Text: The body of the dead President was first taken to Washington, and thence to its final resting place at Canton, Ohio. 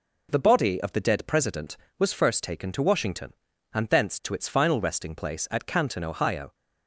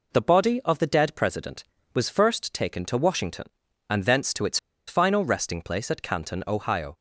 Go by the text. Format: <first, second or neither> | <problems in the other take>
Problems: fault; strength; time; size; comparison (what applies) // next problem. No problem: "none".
first | pauses between "its" and "final"; slight; at 4.5 s; 0.29 s long